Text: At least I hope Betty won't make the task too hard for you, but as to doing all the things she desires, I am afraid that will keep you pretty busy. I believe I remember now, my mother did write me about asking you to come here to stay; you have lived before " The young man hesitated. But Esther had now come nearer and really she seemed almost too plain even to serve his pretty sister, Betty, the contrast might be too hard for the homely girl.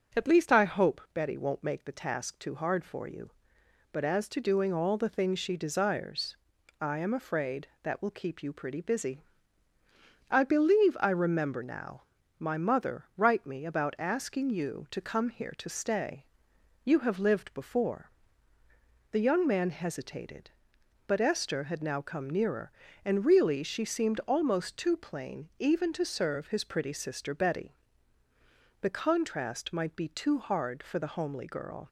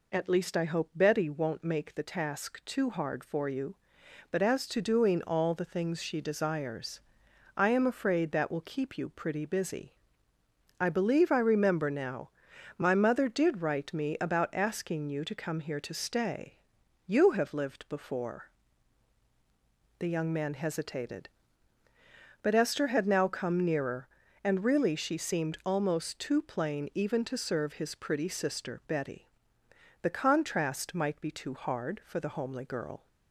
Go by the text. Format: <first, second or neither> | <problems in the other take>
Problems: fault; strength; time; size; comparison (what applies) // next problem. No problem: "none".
second | starts louder than the rest; until 1.2 s; 6.5 dB // skips "did"; at 13.1 s